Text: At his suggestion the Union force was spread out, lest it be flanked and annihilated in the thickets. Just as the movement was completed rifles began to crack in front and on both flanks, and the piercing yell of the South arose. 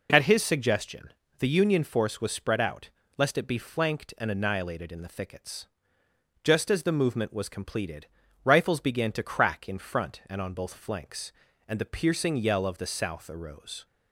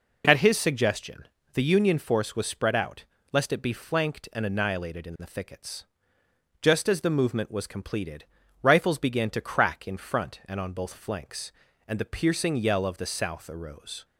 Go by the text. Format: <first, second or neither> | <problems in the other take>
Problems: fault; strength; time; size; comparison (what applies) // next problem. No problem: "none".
neither | pauses between "suggestion" and "the"; slight; the same in both // pauses between "completed" and "rifles"; slight; the same in both